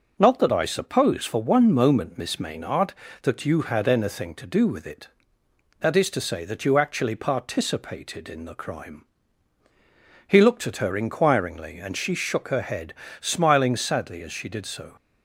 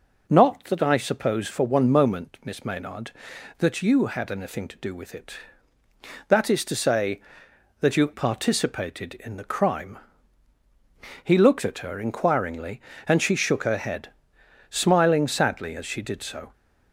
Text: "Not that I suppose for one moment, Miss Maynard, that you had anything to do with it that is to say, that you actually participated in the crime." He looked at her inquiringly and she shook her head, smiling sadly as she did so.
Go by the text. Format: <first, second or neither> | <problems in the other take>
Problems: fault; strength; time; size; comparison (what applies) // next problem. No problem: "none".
first | skips "actually"; at 8.1 s